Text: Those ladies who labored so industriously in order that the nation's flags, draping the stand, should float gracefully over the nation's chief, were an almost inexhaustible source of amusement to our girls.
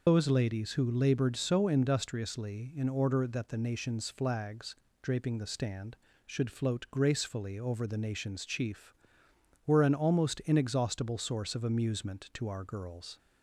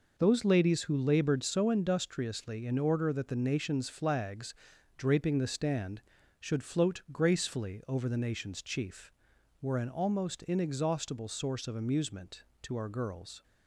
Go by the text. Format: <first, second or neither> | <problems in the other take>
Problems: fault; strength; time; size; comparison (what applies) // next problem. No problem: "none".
second | loses the start of "Those"; at 0.0 s; 155 ms